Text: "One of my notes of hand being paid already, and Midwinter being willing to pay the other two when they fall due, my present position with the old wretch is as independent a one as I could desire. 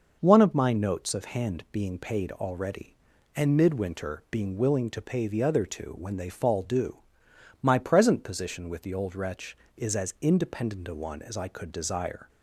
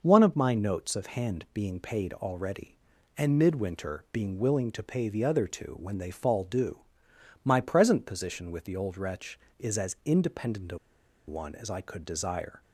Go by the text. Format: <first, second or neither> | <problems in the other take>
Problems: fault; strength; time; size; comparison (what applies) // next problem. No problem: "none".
first | pauses between "a" and "one"; noticeable; at 10.7 s; 0.49 s long